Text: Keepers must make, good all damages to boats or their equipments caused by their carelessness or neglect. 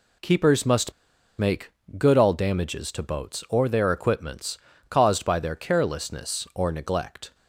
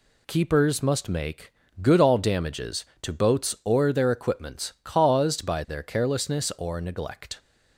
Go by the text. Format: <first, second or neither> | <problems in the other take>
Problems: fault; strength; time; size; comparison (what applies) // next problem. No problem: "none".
second | pauses between "must" and "make"; at 0.9 s; 0.45 s long // pauses between "equipments" and "caused"; slight; at 4.5 s; 0.32 s long